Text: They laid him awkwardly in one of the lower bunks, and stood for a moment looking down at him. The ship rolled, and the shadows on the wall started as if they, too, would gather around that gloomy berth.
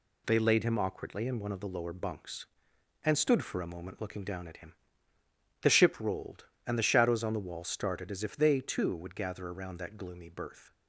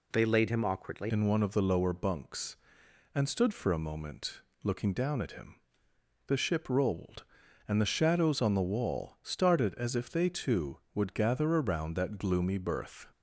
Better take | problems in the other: first | changes voice at "in"; from 1.0 s on; 12.0 s long // pauses between "moment" and "looking"; slight; at 4.4 s; 0.22 s long

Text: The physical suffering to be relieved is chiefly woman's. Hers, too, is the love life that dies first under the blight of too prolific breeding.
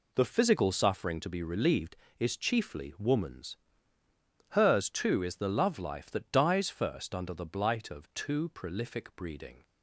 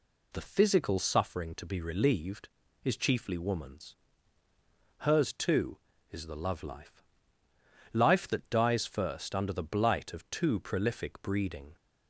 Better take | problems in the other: first | says "life" twice; at 7.9 s

